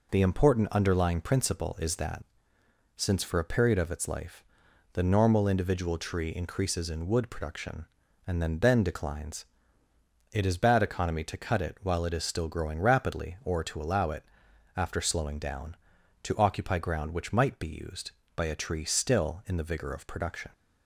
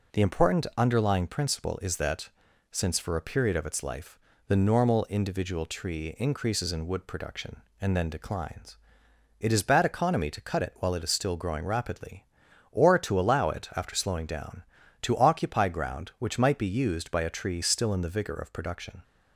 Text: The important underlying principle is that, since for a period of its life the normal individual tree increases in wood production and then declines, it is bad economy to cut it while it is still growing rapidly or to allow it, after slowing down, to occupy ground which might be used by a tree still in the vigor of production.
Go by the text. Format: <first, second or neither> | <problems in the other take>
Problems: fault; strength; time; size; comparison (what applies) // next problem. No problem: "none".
second | pauses between "life" and "the"; noticeable; at 4.4 s; 0.50 s long; slight in the second // says "then" twice; at 8.5 s